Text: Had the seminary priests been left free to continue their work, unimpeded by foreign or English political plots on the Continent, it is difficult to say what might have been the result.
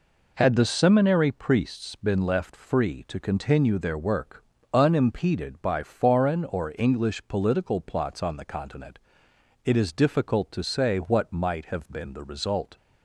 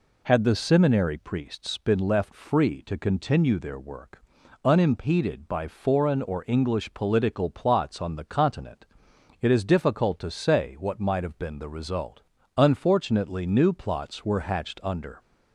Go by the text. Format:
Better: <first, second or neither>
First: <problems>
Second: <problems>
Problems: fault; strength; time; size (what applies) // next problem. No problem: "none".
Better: first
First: none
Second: goes on to say "Unfortunately new plots were hatched under"; strong; from 12.5 s on; 2.6 s long